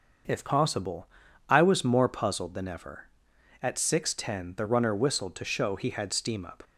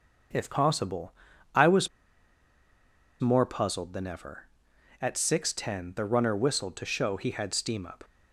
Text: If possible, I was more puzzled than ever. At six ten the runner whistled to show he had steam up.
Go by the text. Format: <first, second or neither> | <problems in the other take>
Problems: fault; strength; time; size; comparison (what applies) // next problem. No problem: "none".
first | starts louder than the rest; until 1.7 s; 6.5 dB; also in the first // pauses between "was" and "more"; strong; at 1.8 s; 1.3 s long